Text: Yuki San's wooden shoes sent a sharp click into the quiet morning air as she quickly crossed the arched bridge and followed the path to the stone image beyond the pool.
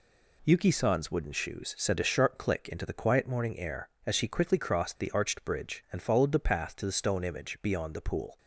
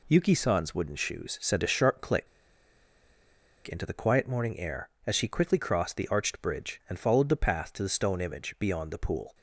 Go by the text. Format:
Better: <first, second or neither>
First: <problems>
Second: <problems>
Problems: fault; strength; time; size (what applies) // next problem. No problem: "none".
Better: first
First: none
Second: pauses between "click" and "into"; strong; at 2.2 s; 1.4 s long